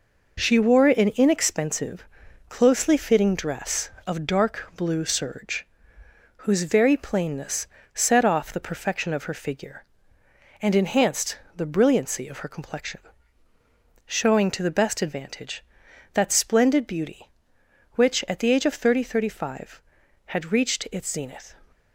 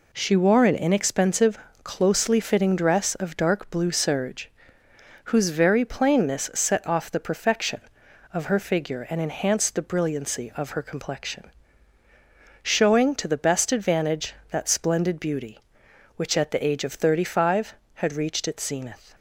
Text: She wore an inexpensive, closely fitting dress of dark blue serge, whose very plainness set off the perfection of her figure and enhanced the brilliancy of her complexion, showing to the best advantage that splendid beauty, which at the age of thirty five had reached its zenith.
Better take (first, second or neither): second